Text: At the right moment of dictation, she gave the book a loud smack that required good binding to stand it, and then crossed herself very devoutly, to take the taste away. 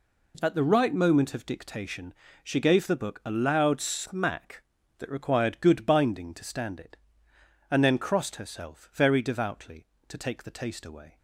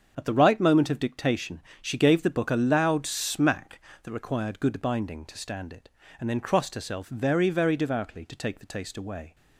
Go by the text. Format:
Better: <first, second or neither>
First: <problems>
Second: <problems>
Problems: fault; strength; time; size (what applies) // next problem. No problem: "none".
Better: first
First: none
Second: starts louder than the rest; until 1.1 s; 7 dB // says "very" twice; at 7.4 s